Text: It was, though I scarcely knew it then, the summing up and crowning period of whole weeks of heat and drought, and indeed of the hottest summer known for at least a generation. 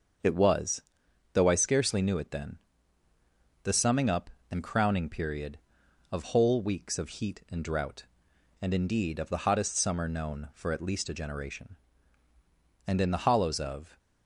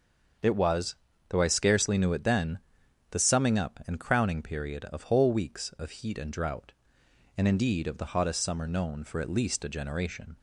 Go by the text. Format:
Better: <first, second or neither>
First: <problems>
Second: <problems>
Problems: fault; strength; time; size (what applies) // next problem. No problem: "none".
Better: second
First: starts louder than the rest; until 1.7 s; 6.5 dB // goes on to say "And in the hollows of"; noticeable; from 12.8 s on; 1.1 s long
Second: starts louder than the rest; until 1.7 s; 6.5 dB